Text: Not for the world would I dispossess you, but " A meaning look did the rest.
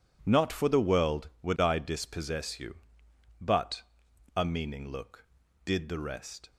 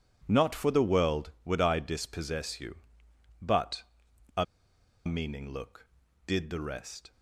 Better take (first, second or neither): first